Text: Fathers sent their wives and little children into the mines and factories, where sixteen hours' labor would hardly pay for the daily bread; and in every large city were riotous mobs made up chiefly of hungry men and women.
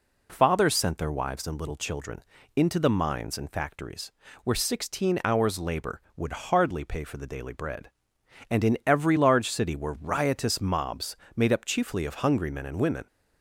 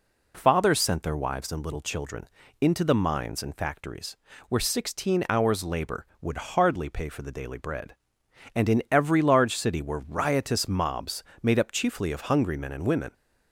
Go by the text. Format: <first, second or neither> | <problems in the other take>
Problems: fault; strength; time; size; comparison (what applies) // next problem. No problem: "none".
neither | pauses between "children" and "into"; slight; the same in both // pauses between "mobs" and "made"; slight; the same in both